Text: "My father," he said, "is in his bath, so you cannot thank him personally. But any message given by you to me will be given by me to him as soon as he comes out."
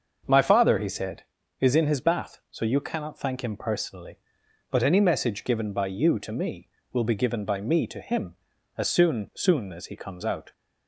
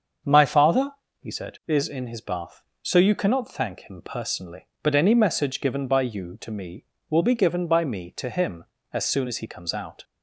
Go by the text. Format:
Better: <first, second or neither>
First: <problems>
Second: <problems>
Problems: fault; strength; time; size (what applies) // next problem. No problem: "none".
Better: second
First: starts louder than the rest; until 1.6 s; 6.5 dB // says "soon" twice; at 9.3 s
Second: starts louder than the rest; until 1.5 s; 7 dB